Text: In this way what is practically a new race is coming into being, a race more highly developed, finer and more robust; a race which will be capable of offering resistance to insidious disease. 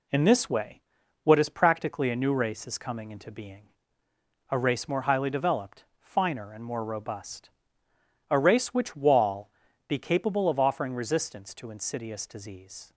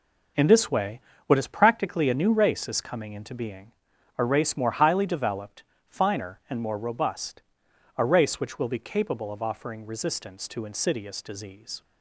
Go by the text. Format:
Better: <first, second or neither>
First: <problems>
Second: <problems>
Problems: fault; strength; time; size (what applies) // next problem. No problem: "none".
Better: second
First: pauses between "way" and "what"; at 0.8 s; 0.42 s long // says "wall" for "will"; at 8.9 s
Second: pauses between "way" and "what"; slight; at 1.0 s; 0.26 s long